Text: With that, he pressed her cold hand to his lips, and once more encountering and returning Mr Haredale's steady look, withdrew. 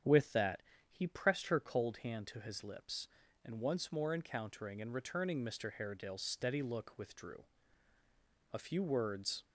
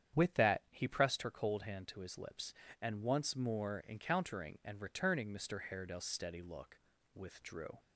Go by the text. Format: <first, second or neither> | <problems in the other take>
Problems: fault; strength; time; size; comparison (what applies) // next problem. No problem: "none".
second | starts louder than the rest; strong; until 1.3 s; 8.5 dB; strong in the second // goes on to say "A few words"; noticeable; from 8.5 s on; 0.92 s long